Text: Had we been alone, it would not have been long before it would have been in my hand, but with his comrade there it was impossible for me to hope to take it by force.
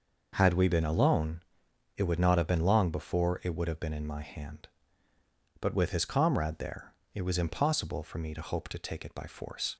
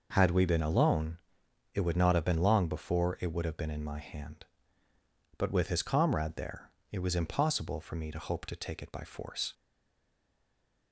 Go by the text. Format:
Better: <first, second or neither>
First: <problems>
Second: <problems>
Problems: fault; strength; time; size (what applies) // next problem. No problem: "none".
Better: first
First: pauses between "there" and "it"; slight; at 6.9 s; 0.22 s long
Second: pauses between "there" and "it"; slight; at 6.6 s; 0.22 s long // stays silent after the last word; noticeable; from 9.5 s on; 1.4 s long